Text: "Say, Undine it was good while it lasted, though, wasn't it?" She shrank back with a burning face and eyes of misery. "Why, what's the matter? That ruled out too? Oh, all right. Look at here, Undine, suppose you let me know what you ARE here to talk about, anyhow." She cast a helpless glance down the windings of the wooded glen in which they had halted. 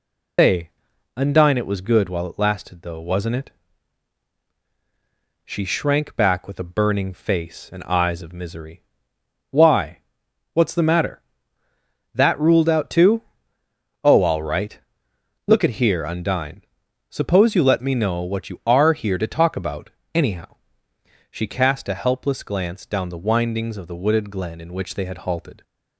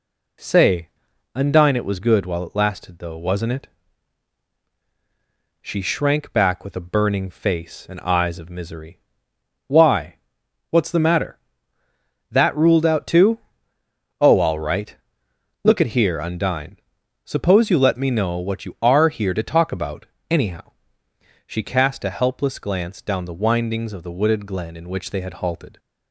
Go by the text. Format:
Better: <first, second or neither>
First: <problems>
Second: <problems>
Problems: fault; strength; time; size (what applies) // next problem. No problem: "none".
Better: second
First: loses the start of "Say"; at 0.3 s; 170 ms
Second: none